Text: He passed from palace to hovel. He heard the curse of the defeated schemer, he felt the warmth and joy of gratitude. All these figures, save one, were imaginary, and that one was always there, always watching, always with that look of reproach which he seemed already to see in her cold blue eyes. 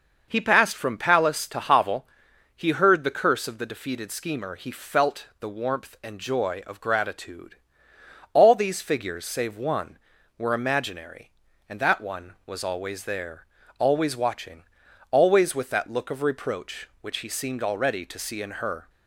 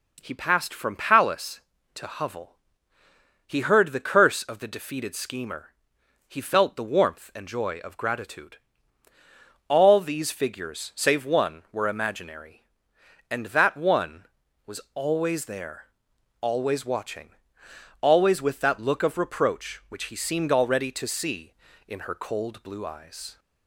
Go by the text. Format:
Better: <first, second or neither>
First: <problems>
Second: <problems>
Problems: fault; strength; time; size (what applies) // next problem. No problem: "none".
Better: second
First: stops before "cold blue eyes"; at 18.8 s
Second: none